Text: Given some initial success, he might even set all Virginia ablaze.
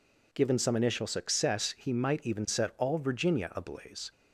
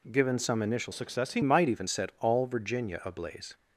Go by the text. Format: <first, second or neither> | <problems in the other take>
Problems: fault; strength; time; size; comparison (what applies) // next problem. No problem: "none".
first | changes voice from "success" to "he"; from 0.9 to 1.4 s; 0.5 s long